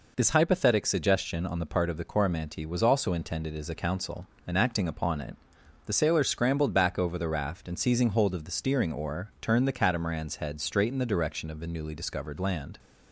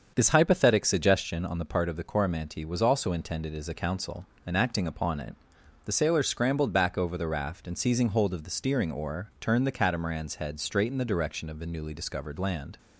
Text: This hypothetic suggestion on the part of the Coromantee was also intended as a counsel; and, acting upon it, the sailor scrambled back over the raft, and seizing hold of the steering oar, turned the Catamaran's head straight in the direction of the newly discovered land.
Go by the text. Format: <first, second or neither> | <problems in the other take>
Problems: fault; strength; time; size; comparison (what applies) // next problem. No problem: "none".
first | starts louder than the rest; until 1.3 s; 7 dB